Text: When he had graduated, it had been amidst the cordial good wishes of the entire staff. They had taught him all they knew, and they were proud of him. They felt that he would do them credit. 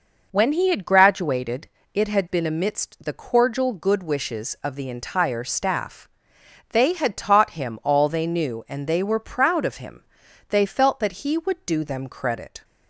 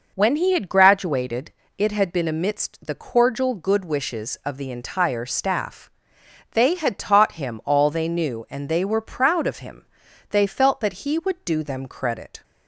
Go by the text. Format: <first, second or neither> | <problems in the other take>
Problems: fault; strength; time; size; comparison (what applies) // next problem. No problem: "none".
neither | none